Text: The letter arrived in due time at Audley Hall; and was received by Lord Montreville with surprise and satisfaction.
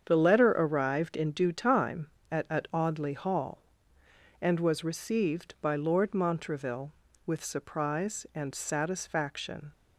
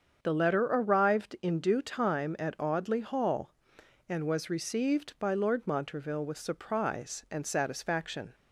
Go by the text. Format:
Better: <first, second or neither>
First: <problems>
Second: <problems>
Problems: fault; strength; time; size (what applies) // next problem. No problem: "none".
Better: second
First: starts louder than the rest; strong; until 1.0 s; 7.5 dB // says "at" twice; at 2.4 s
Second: starts louder than the rest; strong; until 1.2 s; 7 dB